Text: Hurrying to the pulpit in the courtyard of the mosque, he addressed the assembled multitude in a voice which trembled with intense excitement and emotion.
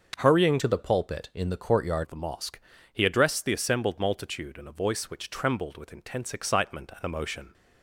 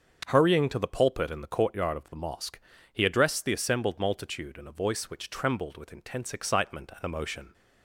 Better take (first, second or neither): second